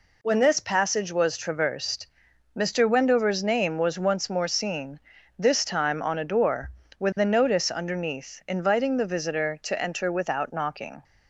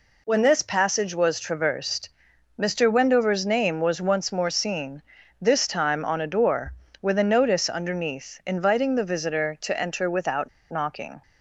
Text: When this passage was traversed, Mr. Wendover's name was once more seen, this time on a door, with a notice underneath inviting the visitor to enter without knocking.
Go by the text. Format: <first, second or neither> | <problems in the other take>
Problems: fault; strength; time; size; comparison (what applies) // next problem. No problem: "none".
first | pauses between "without" and "knocking"; slight; at 10.4 s; 0.20 s long